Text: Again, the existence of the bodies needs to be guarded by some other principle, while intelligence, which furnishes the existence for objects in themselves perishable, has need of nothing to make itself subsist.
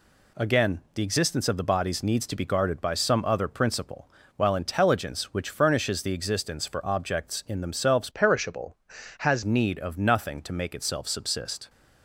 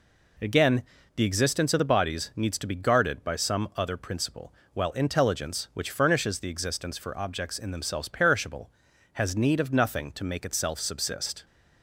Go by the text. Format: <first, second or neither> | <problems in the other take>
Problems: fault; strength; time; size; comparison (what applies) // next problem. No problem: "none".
second | changes voice from "perishable" to "has"; from 8.1 to 9.4 s; 1.3 s long